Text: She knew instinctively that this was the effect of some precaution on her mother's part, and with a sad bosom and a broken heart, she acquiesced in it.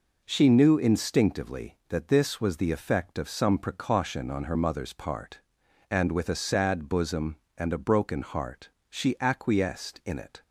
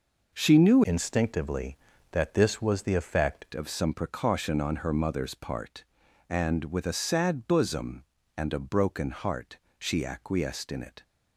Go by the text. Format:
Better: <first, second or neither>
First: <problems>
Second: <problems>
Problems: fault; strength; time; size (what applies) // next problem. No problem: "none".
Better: first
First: none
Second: changes voice from "instinctively" to "effect"; from 0.8 to 3.4 s; 2.6 s long